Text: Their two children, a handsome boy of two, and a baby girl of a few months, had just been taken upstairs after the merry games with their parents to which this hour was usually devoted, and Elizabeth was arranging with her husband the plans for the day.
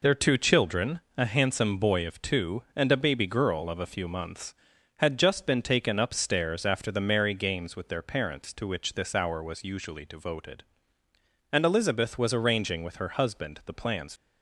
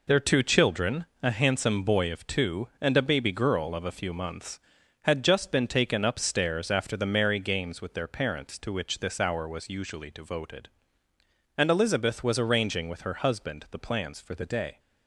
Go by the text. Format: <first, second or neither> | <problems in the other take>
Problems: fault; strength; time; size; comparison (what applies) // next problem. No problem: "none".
second | stops before "for the day"; at 14.1 s